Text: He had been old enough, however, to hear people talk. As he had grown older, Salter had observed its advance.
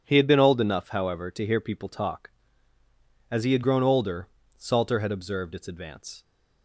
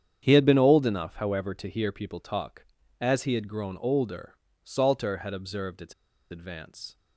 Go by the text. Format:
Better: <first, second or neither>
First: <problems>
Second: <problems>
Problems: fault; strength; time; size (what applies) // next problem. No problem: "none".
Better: first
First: none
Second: starts louder than the rest; strong; until 1.2 s; 8.5 dB // pauses between "its" and "advance"; at 5.9 s; 0.37 s long